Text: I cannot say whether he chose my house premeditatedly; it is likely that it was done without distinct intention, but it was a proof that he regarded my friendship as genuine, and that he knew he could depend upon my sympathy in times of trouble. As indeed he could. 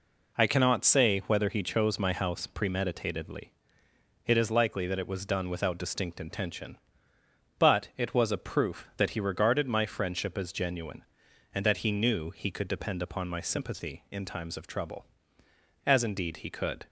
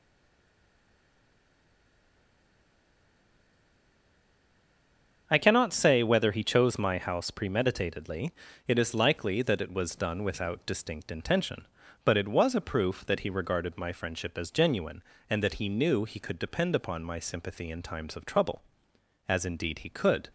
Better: first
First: none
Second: stays silent before the first word; strong; until 5.2 s; 5.2 s long // starts louder than the rest; until 6.2 s; 7 dB

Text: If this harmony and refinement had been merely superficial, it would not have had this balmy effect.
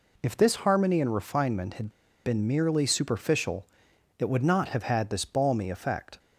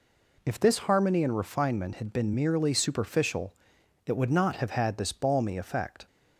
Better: second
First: pauses between "had" and "been"; slight; at 1.9 s; 0.32 s long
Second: none

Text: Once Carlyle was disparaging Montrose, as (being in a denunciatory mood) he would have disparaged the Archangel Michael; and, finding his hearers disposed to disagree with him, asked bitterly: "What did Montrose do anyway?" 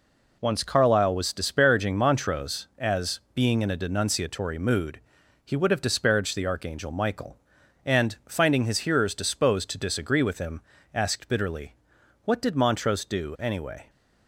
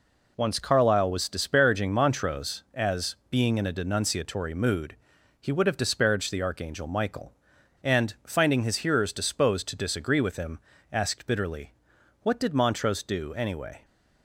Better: neither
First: none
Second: none

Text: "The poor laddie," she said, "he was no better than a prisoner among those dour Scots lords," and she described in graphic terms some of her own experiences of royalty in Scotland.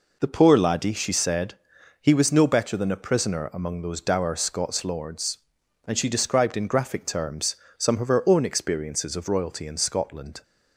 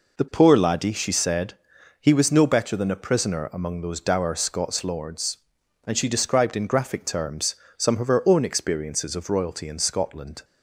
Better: neither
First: pauses between "terms" and "some"; slight; at 7.5 s; 0.22 s long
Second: pauses between "terms" and "some"; slight; at 7.5 s; 0.22 s long

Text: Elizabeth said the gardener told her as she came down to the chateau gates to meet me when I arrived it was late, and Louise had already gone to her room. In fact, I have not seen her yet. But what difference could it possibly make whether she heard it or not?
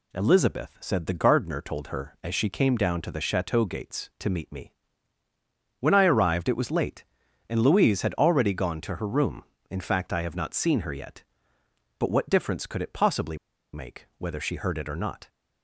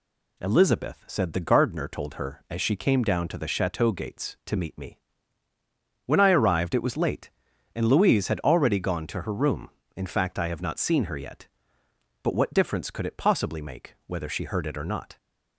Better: second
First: pauses between "me" and "when"; at 4.7 s; 1.0 s long // pauses between "possibly" and "make"; at 13.3 s; 0.36 s long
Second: pauses between "me" and "when"; at 4.9 s; 1.0 s long

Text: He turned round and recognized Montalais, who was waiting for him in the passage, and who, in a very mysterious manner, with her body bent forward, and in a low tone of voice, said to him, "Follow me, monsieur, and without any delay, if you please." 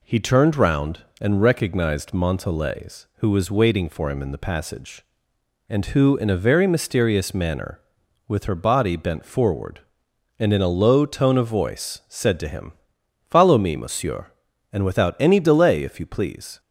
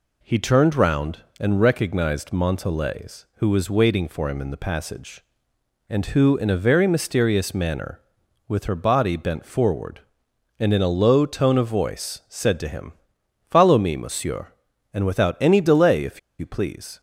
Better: first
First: none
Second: pauses between "if" and "you"; slight; at 16.1 s; 0.20 s long

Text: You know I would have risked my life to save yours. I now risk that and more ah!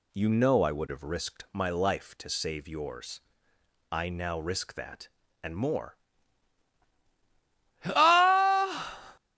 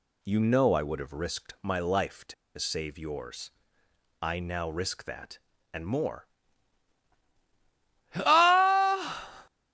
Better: first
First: pauses between "more" and "ah"; strong; at 5.9 s; 1.8 s long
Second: pauses between "to" and "save"; slight; at 2.3 s; 0.23 s long // pauses between "more" and "ah"; strong; at 6.2 s; 1.8 s long

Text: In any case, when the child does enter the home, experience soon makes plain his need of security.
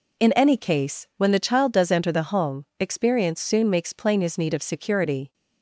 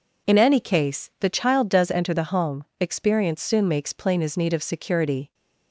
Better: first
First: none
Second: skips "when"; at 1.1 s

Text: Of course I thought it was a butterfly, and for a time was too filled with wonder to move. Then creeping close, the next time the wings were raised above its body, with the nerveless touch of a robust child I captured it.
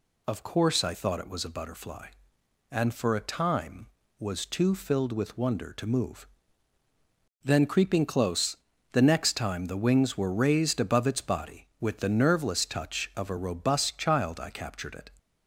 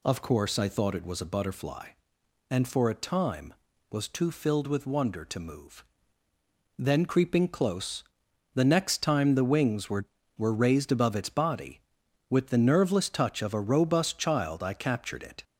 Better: first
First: none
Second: says "were" twice; at 10.3 s

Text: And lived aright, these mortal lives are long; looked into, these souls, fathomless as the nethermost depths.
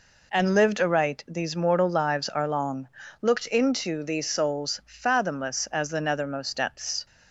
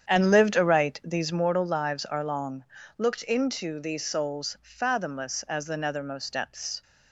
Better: first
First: none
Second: starts louder than the rest; strong; until 1.5 s; 8.5 dB

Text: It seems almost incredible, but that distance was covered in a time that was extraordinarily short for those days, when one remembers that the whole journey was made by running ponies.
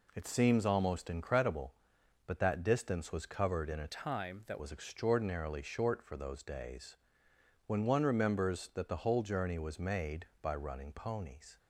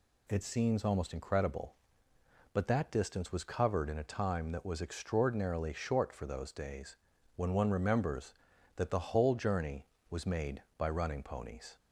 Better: second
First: changes voice from "time" to "that"; from 3.8 to 4.5 s; 0.7 s long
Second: none

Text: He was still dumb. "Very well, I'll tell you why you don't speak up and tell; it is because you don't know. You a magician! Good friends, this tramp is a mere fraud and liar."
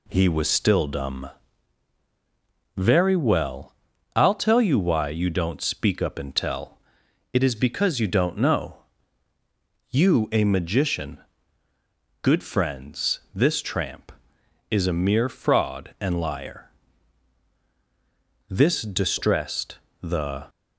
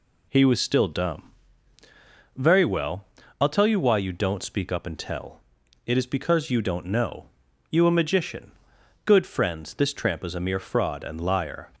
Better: second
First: goes on to say "This distressed the"; strong; from 18.4 s on; 1.9 s long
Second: none

